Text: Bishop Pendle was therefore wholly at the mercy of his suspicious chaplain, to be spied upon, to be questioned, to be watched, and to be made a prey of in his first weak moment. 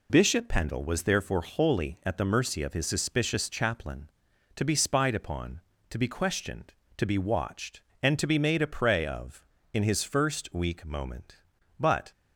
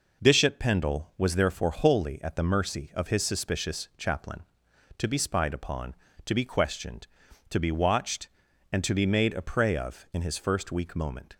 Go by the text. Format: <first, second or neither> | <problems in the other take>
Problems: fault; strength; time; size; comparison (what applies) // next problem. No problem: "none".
second | goes on to say "But"; slight; from 11.7 s on; 0.32 s long